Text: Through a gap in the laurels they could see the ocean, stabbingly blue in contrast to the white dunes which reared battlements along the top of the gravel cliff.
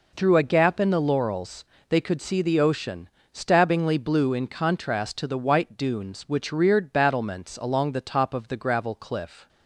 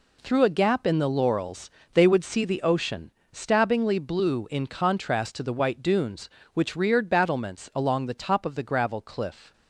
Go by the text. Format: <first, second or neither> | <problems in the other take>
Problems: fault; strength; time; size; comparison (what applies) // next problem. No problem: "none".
first | pauses between "laurels" and "they"; slight; at 1.7 s; 0.22 s long; slight in the first // says "would" for "could"; at 2.0 s